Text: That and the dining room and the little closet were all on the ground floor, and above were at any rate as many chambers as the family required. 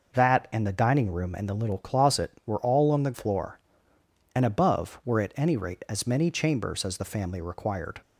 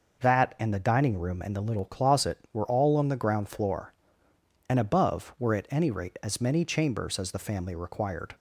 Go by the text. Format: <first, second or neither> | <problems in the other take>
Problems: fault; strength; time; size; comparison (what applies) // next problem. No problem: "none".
second | skips "ground"; at 3.1 s